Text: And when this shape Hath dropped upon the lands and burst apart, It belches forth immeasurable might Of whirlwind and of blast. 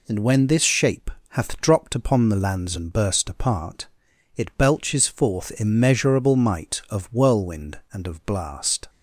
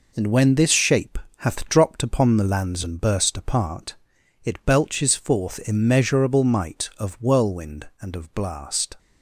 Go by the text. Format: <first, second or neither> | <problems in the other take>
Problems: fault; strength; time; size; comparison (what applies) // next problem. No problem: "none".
first | gets quieter; throughout; 6.5 dB // pauses between "shape" and "Hath"; slight; at 1.1 s; 0.20 s long; slight in the first